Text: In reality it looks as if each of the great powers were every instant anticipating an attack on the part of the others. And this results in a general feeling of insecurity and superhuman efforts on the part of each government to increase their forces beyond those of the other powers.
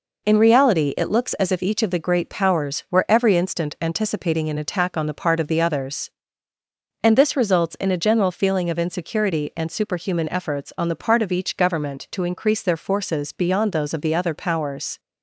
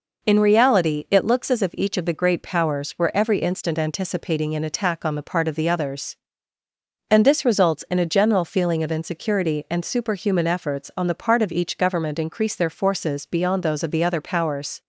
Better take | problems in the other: first | skips "to"; at 12.1 s

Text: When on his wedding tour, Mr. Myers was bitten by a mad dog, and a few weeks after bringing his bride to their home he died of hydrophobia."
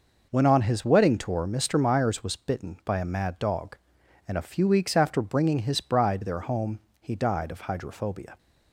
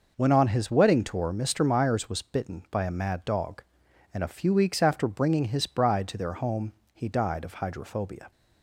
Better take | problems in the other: second | skips "to"; at 6.2 s // pauses between "home" and "he"; slight; at 6.7 s; 0.20 s long; slight in the second

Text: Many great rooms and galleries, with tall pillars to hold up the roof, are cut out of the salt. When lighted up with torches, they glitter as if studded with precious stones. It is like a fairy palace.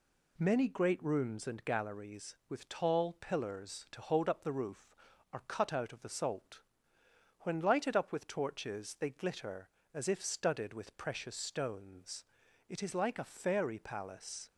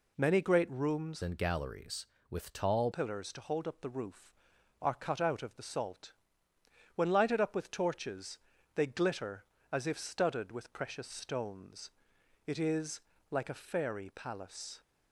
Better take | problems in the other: first | changes voice from "and" to "tall"; from 1.2 to 2.9 s; 1.7 s long // pauses between "is" and "like"; slight; at 13.0 s; 0.30 s long

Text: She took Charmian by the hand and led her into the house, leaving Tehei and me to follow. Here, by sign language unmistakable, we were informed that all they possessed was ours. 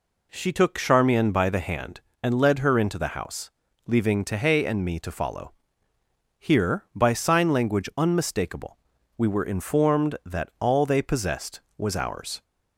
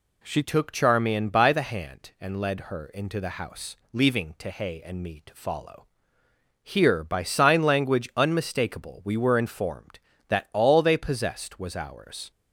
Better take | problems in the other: first | changes voice at "took"; from 0.4 s on; 11.9 s long

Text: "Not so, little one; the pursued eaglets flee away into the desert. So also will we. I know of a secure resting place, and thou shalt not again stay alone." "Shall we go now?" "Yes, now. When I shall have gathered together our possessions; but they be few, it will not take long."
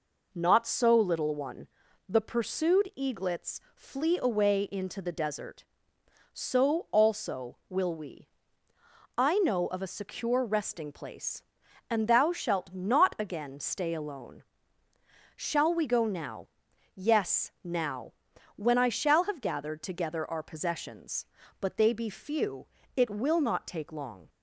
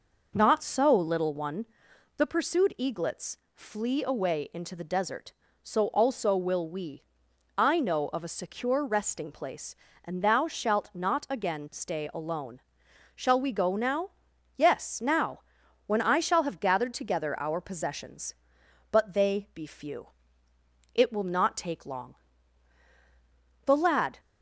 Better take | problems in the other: first | pauses between "eaglets" and "flee"; slight; at 3.3 s; 0.18 s long; slight in the first // goes on to say "The lad"; from 23.6 s on; 0.54 s long

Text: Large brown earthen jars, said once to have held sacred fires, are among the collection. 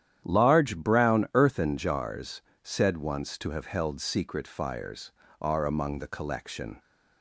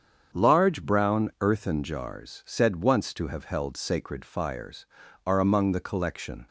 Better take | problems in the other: second | starts louder than the rest; strong; until 1.2 s; 10.5 dB; strong in the second // says "secret" for "sacred"; at 3.9 s

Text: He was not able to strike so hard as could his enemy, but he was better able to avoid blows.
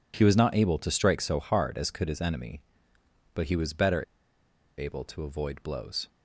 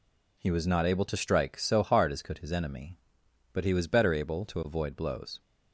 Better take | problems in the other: second | pauses between "better" and "able"; noticeable; at 4.0 s; 0.75 s long

